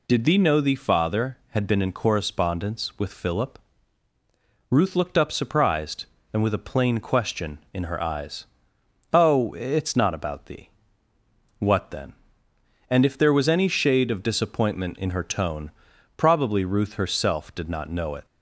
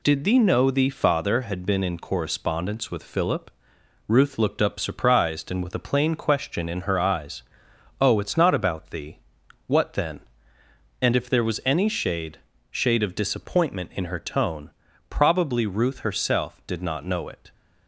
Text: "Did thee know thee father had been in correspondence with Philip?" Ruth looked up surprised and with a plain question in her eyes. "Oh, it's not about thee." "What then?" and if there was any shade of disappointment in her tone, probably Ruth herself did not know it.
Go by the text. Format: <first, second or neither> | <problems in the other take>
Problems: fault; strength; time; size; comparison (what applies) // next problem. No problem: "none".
first | says "shade" twice; at 12.6 s